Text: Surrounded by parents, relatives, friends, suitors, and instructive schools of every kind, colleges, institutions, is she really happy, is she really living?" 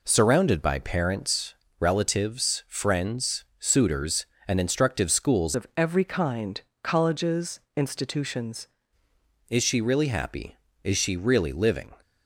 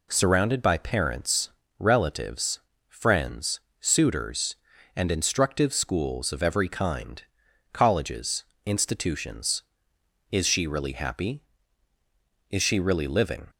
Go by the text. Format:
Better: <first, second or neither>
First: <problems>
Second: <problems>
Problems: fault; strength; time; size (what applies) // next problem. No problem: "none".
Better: second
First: changes voice from "of" to "institutions"; from 5.5 to 8.6 s; 3.1 s long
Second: none